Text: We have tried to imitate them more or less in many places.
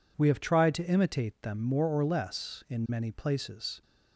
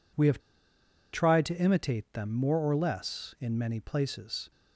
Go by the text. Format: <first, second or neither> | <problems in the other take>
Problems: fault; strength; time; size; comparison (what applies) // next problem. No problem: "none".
first | pauses between "have" and "tried"; noticeable; at 0.3 s; 0.74 s long